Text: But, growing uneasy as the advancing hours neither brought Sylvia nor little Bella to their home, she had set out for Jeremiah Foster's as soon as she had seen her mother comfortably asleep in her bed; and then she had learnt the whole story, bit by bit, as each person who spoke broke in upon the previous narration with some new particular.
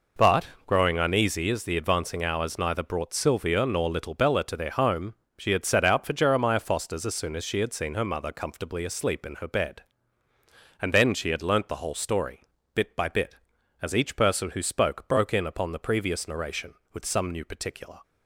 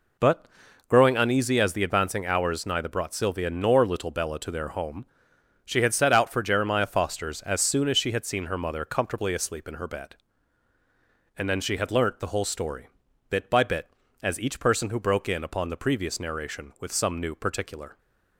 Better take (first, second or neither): first